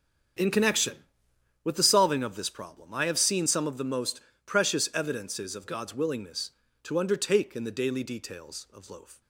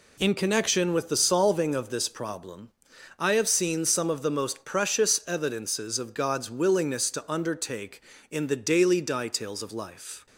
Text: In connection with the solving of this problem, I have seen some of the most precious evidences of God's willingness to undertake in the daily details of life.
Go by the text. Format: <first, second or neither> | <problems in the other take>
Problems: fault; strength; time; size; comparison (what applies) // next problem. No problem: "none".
second | starts louder than the rest; strong; until 2.0 s; 8 dB // pauses between "most" and "precious"; slight; at 4.1 s; 0.24 s long // says "loaf" for "life"; at 8.9 s